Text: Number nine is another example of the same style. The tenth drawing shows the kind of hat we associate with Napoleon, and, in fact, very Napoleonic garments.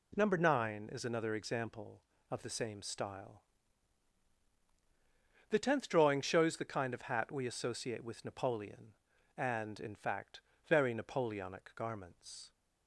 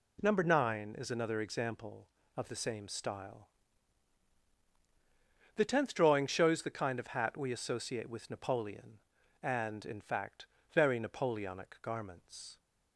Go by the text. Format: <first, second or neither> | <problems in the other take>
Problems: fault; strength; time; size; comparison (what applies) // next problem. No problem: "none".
neither | none